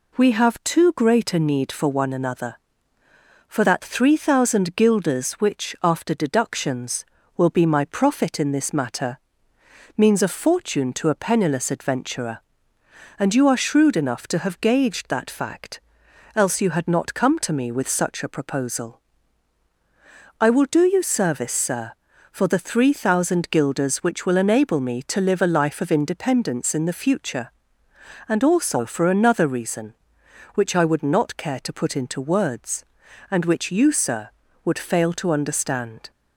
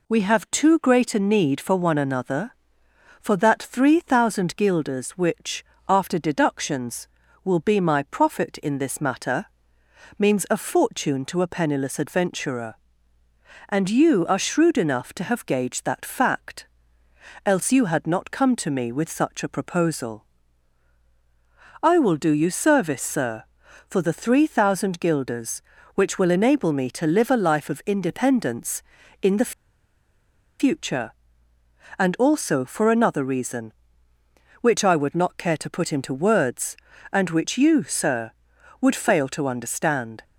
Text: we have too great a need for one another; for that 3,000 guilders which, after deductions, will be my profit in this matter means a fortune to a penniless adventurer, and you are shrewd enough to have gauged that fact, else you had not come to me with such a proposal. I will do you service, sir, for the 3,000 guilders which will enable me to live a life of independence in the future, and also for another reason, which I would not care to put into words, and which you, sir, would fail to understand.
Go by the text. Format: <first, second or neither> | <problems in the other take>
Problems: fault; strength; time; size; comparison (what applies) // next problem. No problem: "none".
first | pauses between "matter" and "means"; noticeable; at 9.4 s; 0.72 s long; noticeable in the first // pauses between "the" and "future"; at 29.5 s; 1.0 s long